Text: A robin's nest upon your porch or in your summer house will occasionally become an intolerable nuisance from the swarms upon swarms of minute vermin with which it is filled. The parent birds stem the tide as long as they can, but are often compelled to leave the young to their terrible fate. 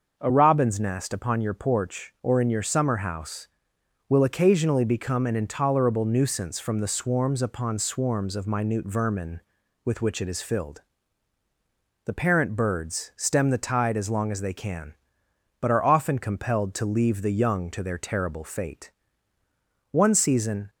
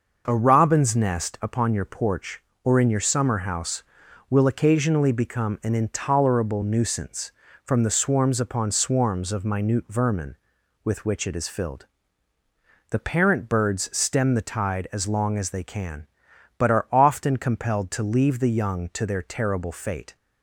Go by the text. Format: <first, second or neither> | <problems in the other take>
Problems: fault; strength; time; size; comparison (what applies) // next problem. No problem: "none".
second | starts louder than the rest; until 1.1 s; 6 dB // goes on to say "One season"; noticeable; from 19.9 s on; 0.78 s long